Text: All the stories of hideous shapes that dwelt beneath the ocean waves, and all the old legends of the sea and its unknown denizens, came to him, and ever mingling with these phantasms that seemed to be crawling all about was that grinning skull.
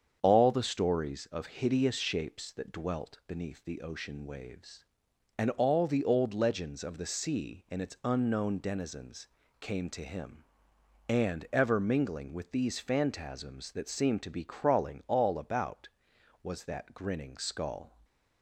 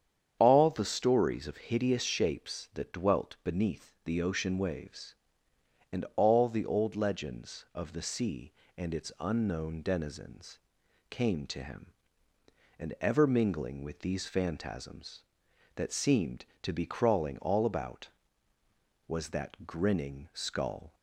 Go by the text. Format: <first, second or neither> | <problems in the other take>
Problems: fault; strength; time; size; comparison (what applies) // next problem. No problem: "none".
neither | starts louder than the rest; strong; the same in both